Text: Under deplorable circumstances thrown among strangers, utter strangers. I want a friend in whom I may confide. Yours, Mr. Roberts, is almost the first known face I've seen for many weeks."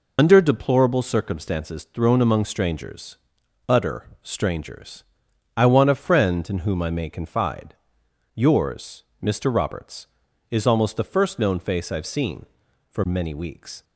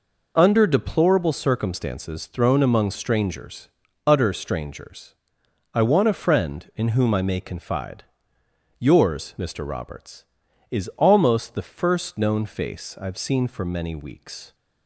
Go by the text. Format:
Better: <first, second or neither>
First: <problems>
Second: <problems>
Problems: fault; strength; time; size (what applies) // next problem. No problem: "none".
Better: second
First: loses the start of "Under"; at 0.1 s; 65 ms // pauses between "utter" and "strangers"; slight; at 4.0 s; 0.16 s long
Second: none